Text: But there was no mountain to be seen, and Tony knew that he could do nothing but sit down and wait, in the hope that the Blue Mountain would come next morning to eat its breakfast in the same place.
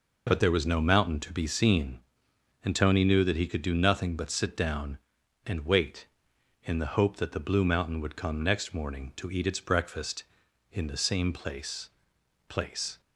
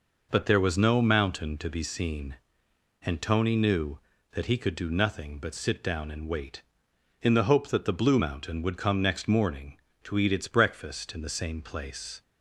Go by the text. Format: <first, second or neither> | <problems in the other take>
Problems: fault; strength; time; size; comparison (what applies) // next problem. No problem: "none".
second | says "place" twice; at 12.4 s